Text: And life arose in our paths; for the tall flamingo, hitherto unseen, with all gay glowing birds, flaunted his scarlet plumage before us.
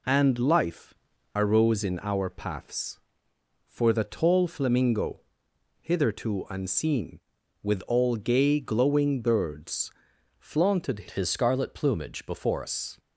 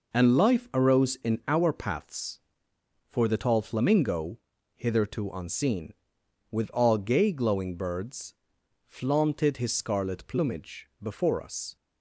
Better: second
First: pauses between "life" and "arose"; at 0.9 s; 0.42 s long // changes voice from "his" to "before"; from 11.0 to 12.6 s; 1.6 s long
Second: none

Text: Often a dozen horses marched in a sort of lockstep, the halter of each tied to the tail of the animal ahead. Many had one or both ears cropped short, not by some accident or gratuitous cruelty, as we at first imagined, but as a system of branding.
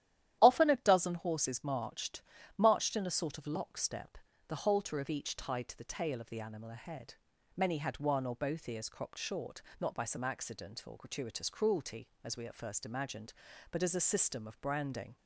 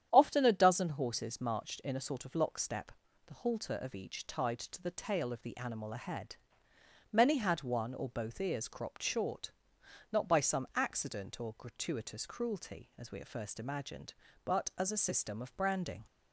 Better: second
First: starts louder than the rest; strong; until 1.4 s; 12 dB // says "marched" twice; at 2.5 s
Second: starts louder than the rest; strong; until 1.1 s; 9.5 dB

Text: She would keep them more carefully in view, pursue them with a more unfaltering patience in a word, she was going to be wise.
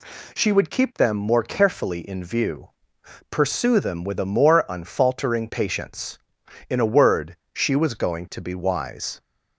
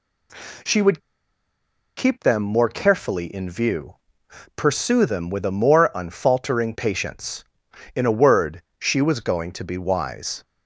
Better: first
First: none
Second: pauses between "would" and "keep"; noticeable; at 1.0 s; 0.96 s long

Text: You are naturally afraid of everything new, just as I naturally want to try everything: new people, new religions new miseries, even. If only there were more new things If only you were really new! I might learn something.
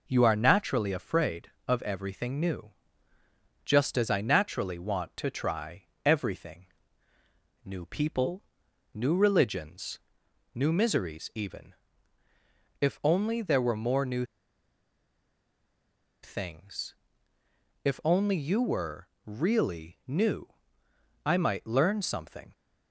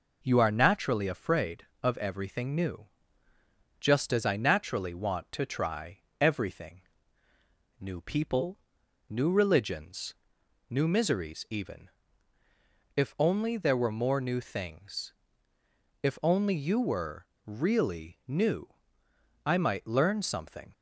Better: second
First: pauses between "try" and "everything"; slight; at 5.8 s; 0.22 s long // pauses between "religions" and "new"; noticeable; at 9.9 s; 0.56 s long // pauses between "new" and "things"; strong; at 14.2 s; 1.9 s long // pauses between "things" and "If"; noticeable; at 16.9 s; 0.92 s long // pauses between "were" and "really"; slight; at 19.0 s; 0.16 s long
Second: pauses between "try" and "everything"; slight; at 5.9 s; 0.22 s long // pauses between "religions" and "new"; noticeable; at 10.1 s; 0.56 s long // pauses between "things" and "If"; noticeable; at 15.1 s; 0.92 s long // pauses between "were" and "really"; slight; at 17.2 s; 0.17 s long

